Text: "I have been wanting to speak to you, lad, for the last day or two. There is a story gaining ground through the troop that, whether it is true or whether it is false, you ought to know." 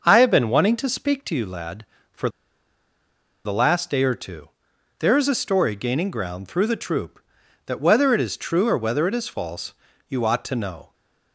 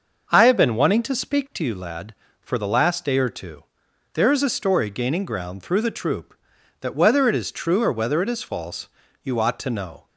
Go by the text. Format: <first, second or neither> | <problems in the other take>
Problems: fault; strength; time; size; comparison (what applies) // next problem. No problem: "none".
second | starts louder than the rest; noticeable; until 1.0 s; 6 dB; noticeable in the second // pauses between "for" and "the"; at 2.2 s; 1.1 s long